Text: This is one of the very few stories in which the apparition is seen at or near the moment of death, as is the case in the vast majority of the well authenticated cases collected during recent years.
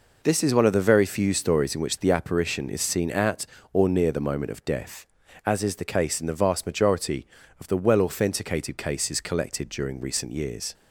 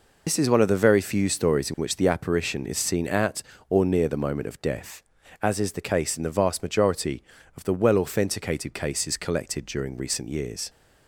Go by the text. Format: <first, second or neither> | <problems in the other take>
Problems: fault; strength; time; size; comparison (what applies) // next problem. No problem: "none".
first | loses the start of "This"; at 0.2 s; 85 ms